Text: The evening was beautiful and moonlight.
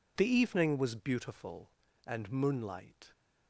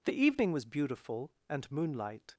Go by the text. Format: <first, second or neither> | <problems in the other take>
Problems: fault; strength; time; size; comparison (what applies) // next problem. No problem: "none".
neither | none